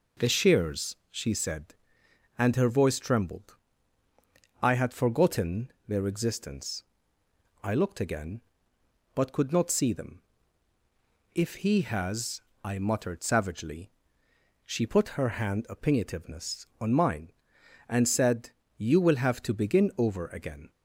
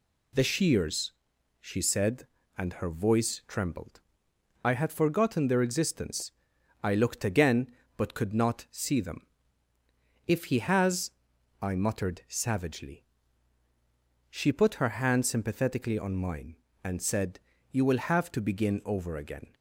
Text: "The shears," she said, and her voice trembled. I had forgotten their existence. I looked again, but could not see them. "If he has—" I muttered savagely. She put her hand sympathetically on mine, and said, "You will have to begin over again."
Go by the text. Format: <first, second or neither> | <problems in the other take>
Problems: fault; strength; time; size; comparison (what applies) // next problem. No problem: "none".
second | says "opinionativeness" for "sympathetically"; at 15.6 s